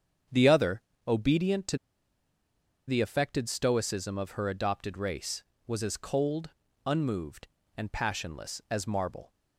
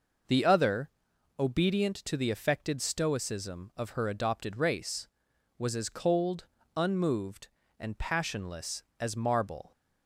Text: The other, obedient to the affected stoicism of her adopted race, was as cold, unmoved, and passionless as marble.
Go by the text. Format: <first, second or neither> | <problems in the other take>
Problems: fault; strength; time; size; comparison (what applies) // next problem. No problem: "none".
second | starts louder than the rest; strong; until 1.5 s; 7.5 dB // pauses between "to" and "the"; at 1.7 s; 1.1 s long